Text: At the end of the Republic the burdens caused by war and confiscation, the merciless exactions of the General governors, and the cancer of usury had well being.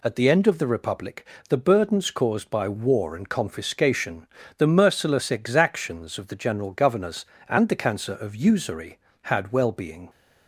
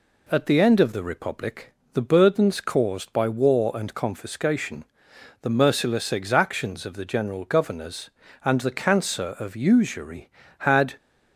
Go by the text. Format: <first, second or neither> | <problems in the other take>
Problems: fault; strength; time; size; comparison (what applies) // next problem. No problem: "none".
first | pauses between "Republic" and "the"; slight; at 1.7 s; 0.22 s long; slight in the first // stops before "well being"; at 10.9 s